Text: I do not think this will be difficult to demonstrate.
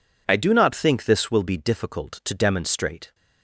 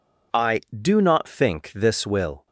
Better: first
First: none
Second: stops before "be difficult to demonstrate"; at 2.4 s

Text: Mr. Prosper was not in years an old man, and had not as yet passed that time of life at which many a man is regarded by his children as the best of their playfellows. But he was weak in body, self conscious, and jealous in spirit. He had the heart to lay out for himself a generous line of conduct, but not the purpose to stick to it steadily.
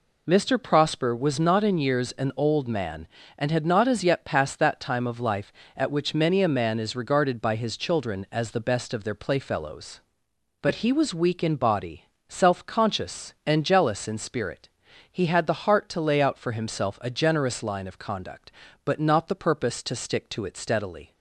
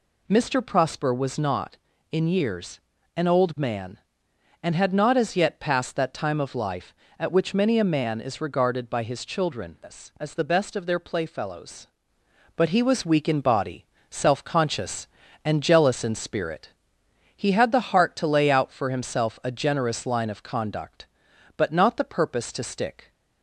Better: first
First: none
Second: pauses between "years" and "an"; slight; at 2.7 s; 0.36 s long // stops before "to it steadily"; at 23.1 s

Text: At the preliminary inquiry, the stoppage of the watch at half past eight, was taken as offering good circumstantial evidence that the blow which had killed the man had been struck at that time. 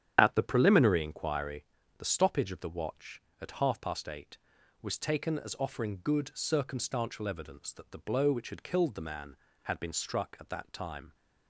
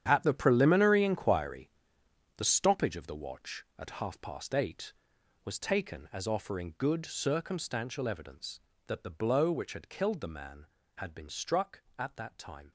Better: first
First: starts louder than the rest; strong; until 1.2 s; 8 dB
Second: gets quieter; strong; throughout; 13 dB // starts louder than the rest; strong; until 1.0 s; 9.5 dB

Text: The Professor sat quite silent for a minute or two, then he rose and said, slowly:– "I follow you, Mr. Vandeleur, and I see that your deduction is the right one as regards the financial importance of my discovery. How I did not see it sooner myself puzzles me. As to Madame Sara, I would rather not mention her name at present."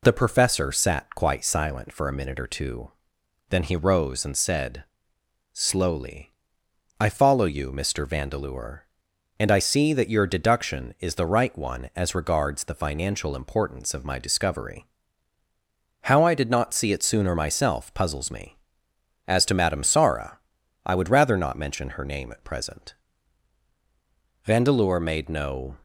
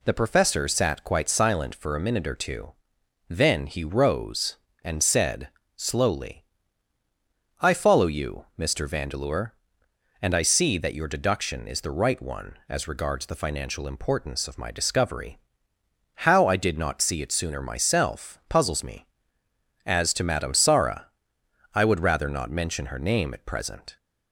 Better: second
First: goes on to say "Vandeleur made no"; from 24.4 s on; 1.3 s long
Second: none

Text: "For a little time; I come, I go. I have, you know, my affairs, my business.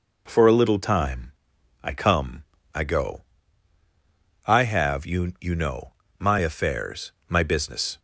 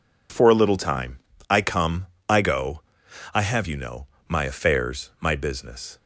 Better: second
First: says "you" twice; at 5.3 s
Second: none

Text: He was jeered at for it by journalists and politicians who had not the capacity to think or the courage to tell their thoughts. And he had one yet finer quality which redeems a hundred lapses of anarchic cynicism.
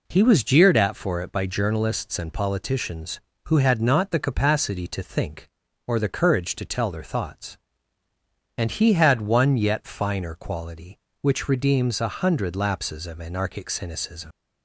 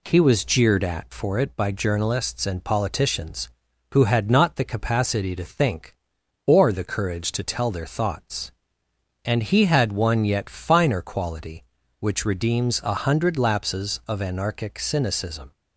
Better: second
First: leaves "cynicism" unfinished; at 14.3 s; 85 ms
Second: none

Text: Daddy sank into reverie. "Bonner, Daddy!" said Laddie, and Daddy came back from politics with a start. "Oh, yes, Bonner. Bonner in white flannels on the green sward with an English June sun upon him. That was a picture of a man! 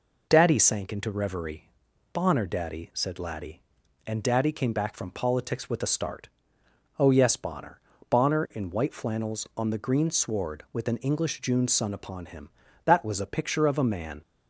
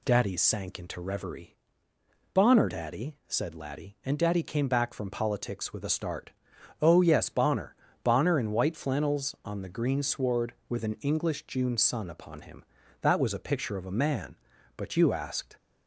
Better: first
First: none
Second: goes on to say "But you asked"; noticeable; from 14.7 s on; 0.80 s long

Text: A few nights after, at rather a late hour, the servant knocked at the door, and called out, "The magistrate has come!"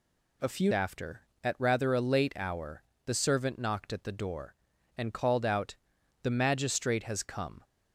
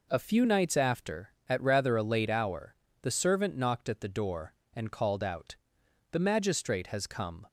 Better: second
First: skips "nights"; at 0.7 s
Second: none

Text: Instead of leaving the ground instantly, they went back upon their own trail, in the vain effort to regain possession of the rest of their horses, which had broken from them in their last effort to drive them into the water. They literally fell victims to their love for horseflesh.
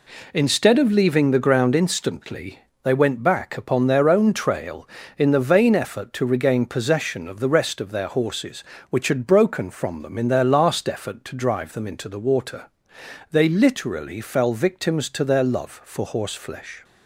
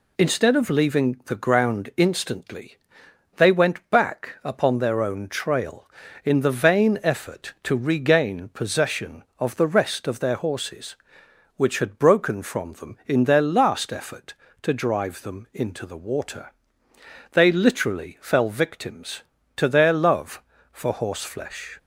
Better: neither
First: none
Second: none

